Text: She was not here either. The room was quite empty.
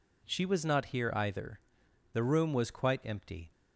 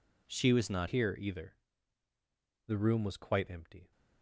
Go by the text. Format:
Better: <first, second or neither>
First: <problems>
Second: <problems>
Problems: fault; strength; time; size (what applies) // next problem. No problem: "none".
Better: first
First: none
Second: changes voice at "here"; from 0.8 s on; 3.1 s long